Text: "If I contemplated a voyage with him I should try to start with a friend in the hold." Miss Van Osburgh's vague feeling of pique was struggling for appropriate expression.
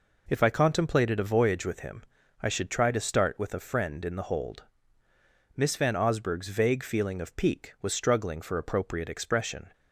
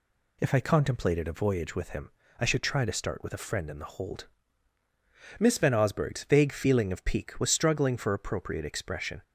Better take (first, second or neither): neither